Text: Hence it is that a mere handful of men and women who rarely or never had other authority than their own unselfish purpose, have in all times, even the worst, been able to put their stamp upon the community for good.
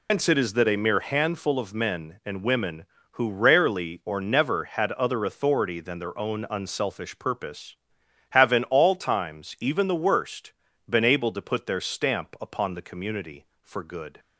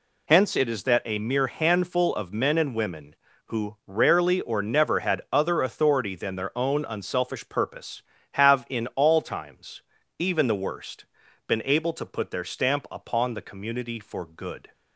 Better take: second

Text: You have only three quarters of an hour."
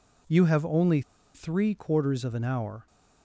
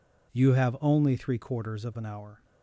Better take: second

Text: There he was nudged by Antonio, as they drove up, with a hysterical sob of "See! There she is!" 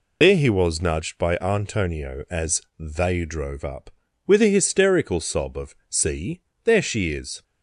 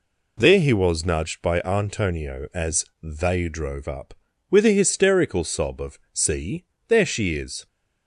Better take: second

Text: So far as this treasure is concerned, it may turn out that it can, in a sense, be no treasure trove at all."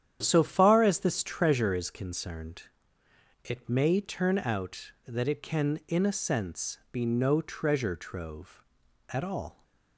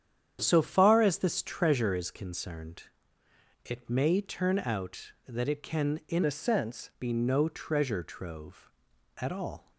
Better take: first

